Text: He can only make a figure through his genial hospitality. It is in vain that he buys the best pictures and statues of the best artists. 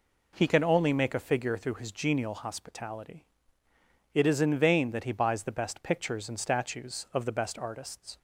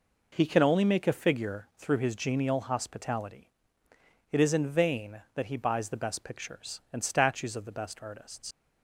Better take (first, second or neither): first